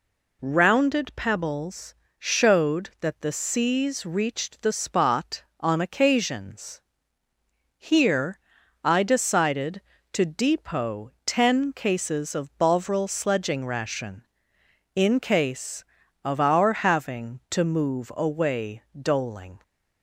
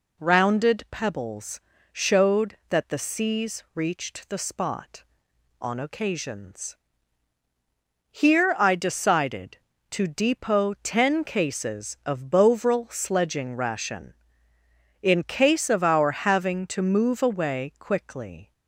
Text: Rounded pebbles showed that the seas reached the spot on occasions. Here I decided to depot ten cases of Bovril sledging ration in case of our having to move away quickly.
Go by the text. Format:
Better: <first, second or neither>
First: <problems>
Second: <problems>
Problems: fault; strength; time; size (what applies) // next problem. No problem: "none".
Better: second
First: pauses between "pebbles" and "showed"; slight; at 1.9 s; 0.24 s long // pauses between "Here" and "I"; at 8.3 s; 0.44 s long // says "doling" for "quickly"; at 18.9 s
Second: pauses between "pebbles" and "showed"; slight; at 1.5 s; 0.32 s long